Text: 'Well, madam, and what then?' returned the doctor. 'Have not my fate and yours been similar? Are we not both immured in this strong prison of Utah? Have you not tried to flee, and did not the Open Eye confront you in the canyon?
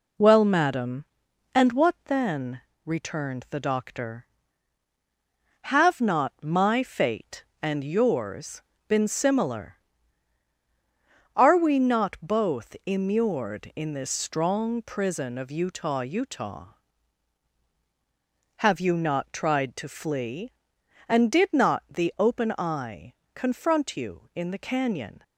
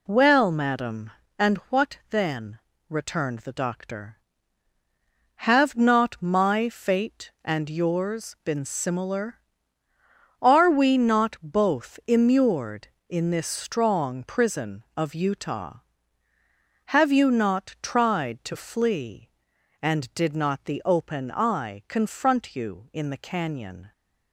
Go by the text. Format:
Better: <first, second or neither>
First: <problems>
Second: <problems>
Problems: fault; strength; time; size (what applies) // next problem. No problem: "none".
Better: second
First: pauses between "yours" and "been"; slight; at 8.6 s; 0.26 s long // says "Utah" twice; at 16.0 s // pauses between "Eye" and "confront"; slight; at 23.1 s; 0.22 s long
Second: none